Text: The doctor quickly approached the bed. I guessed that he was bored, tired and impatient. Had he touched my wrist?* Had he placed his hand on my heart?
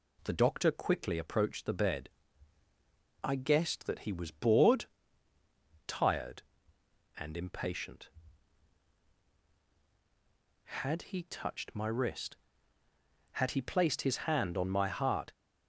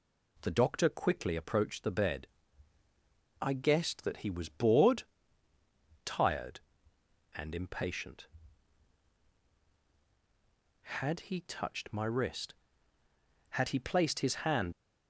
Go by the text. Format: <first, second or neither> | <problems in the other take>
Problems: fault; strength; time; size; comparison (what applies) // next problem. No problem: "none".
first | stops before "on my heart"; at 14.7 s